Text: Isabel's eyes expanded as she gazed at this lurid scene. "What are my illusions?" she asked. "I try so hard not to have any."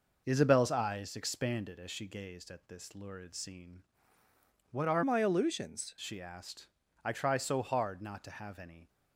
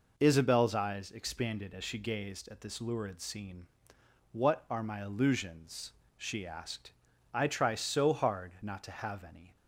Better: second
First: changes voice from "my" to "illusions"; from 5.0 to 5.9 s; 0.9 s long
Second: none

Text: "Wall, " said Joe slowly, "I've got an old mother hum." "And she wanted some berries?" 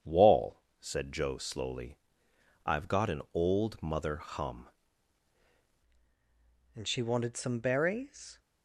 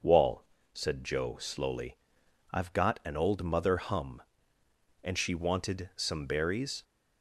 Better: second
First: starts louder than the rest; strong; until 1.1 s; 8 dB // changes voice at "And"; from 6.7 s on; 1.6 s long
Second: starts louder than the rest; noticeable; until 1.1 s; 6 dB

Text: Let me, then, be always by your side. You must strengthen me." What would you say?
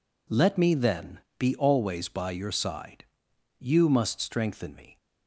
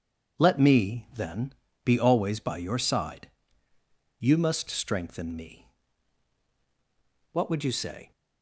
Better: second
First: stops before "What would you say"; at 4.9 s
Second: none

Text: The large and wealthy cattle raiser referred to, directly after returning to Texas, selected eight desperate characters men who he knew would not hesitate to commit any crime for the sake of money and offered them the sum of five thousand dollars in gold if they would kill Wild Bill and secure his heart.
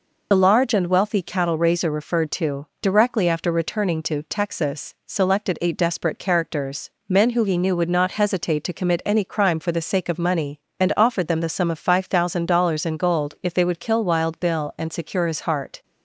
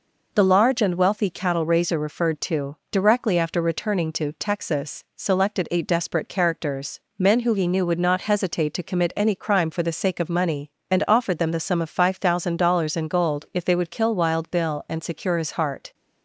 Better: second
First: loses the start of "The"; at 0.3 s; 55 ms // pauses between "characters" and "men"; slight; at 6.8 s; 0.16 s long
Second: pauses between "characters" and "men"; slight; at 6.9 s; 0.16 s long

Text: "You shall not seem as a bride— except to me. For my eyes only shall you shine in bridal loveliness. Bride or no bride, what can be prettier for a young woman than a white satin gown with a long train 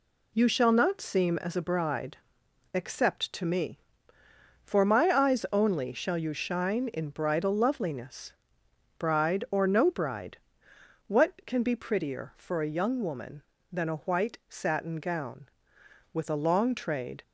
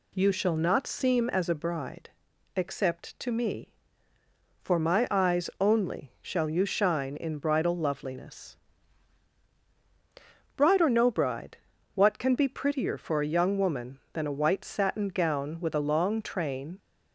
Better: second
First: says "trade" for "train"; at 16.7 s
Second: none

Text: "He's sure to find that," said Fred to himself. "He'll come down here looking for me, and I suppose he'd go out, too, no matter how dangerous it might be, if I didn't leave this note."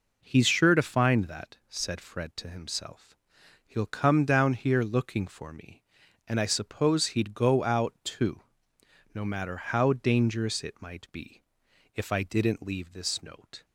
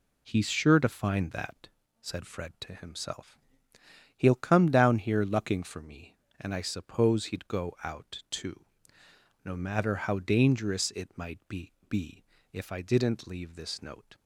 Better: first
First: none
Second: says "be" twice; at 11.9 s

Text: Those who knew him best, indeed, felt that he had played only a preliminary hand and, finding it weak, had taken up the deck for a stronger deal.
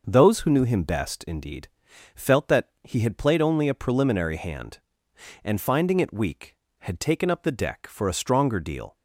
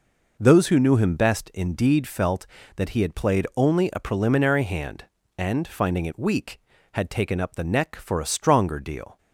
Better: first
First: none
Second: says "neck" for "deck"; at 7.6 s

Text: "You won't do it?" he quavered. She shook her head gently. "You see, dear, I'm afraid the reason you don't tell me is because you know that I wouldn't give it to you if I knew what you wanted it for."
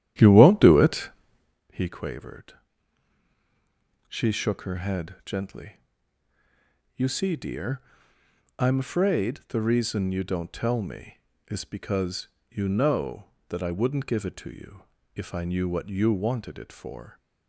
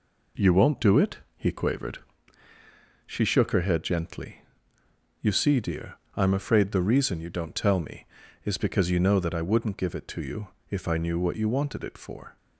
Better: second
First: starts louder than the rest; strong; until 1.7 s; 11 dB // pauses between "because" and "you"; slight; at 12.2 s; 0.22 s long // pauses between "you" and "if"; slight; at 14.8 s; 0.30 s long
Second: pauses between "you" and "if"; slight; at 10.4 s; 0.20 s long

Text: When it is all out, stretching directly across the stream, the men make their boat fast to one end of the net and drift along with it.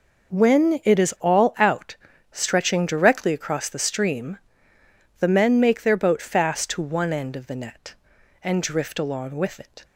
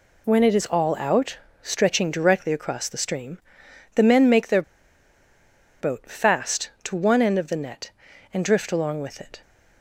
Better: first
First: none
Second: pauses between "their" and "boat"; at 4.6 s; 1.1 s long

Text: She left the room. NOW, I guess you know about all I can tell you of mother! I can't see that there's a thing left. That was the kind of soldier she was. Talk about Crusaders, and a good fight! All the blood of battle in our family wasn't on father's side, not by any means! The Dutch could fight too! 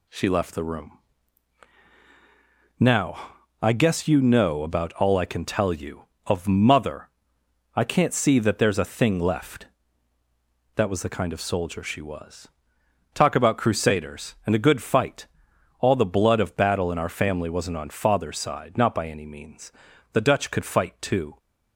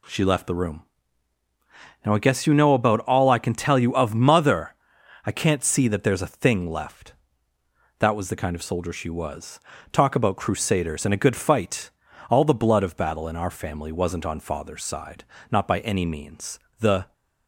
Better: first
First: none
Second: stops before "Dutch could fight too"; at 17.1 s

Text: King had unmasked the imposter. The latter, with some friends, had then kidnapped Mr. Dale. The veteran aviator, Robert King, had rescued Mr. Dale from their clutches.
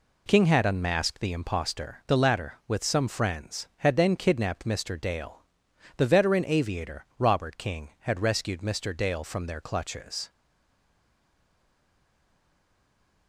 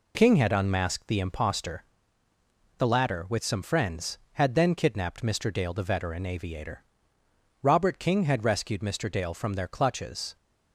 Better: second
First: stays silent after the last word; strong; from 10.3 s on; 2.9 s long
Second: none

